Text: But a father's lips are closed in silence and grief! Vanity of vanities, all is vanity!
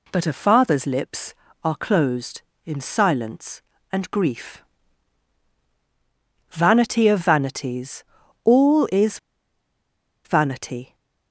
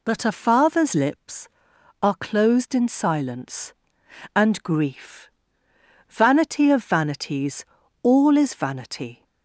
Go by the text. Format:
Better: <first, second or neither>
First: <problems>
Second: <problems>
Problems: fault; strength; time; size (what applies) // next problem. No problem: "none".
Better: second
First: pauses between "is" and "vanity"; at 9.1 s; 1.0 s long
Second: none